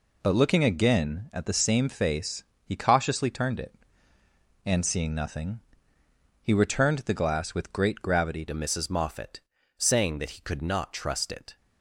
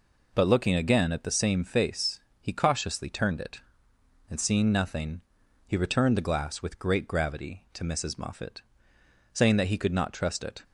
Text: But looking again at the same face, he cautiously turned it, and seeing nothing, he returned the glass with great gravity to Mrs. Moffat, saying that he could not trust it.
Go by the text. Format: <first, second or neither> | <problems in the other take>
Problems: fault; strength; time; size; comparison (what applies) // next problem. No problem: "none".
second | changes voice at "to"; from 8.4 s on; 3.1 s long